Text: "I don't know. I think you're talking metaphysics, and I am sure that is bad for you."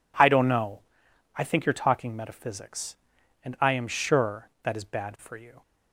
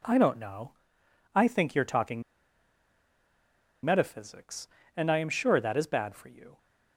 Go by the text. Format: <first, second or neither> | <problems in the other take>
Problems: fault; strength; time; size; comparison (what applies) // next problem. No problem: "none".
first | pauses between "talking" and "metaphysics"; strong; at 2.2 s; 1.6 s long